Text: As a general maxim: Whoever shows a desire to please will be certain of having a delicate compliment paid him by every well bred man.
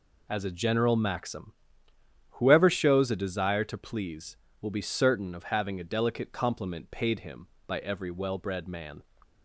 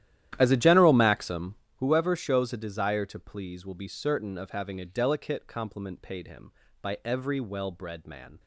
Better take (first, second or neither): first